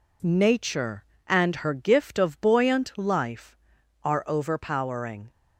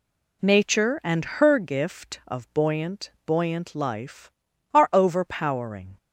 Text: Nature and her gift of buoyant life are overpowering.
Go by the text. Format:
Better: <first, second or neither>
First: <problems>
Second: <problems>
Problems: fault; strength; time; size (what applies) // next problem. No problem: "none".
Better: first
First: none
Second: says "buoyant" twice; at 3.2 s